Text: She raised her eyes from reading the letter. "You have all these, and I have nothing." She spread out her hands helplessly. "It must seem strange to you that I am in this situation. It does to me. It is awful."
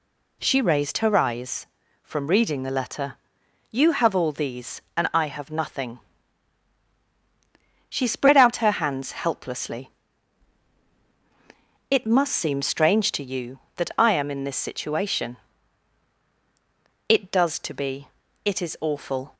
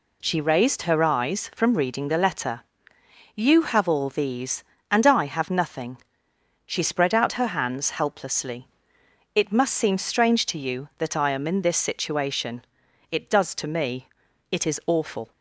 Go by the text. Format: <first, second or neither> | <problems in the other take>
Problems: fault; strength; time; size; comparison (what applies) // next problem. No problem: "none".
second | says "be" for "me"; at 17.7 s